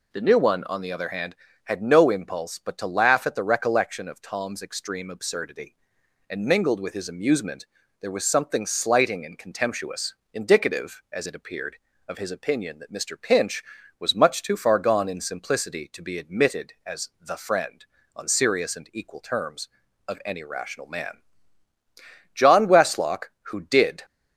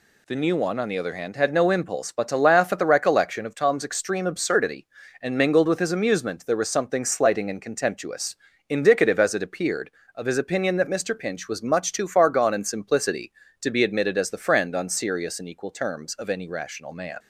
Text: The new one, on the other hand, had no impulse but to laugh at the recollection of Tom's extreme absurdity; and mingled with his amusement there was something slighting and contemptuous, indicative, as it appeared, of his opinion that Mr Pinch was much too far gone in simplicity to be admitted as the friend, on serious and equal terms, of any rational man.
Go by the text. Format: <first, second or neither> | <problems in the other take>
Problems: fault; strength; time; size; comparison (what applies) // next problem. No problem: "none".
second | pauses between "amusement" and "there"; at 7.6 s; 0.38 s long // goes on to say "John Westlock who did"; from 22.3 s on; 1.6 s long